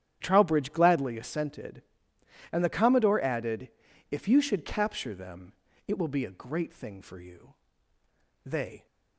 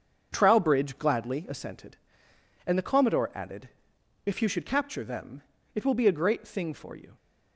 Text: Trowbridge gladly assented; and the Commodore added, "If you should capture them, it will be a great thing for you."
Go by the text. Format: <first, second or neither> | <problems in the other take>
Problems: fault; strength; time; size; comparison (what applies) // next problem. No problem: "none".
second | starts louder than the rest; strong; until 1.2 s; 10 dB; also in the second // goes on to say "They"; slight; from 8.4 s on; 0.40 s long